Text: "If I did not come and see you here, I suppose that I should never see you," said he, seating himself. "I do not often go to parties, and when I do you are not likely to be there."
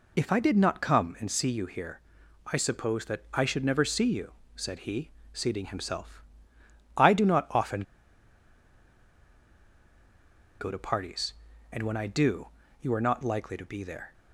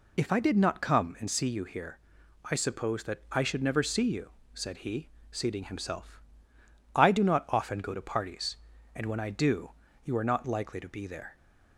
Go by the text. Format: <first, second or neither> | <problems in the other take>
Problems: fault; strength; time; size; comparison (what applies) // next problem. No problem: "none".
second | pauses between "often" and "go"; strong; at 7.8 s; 2.7 s long // pauses between "do" and "you"; slight; at 12.4 s; 0.32 s long; slight in the second